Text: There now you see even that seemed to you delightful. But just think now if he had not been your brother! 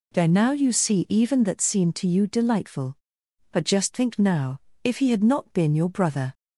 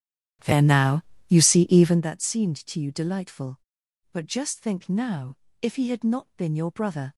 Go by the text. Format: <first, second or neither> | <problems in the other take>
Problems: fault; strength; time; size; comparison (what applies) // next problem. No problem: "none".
first | starts louder than the rest; strong; until 2.1 s; 11 dB // pauses between "now" and "you"; slight; at 1.0 s; 0.28 s long // pauses between "now" and "if"; slight; at 5.3 s; 0.24 s long; slight in the first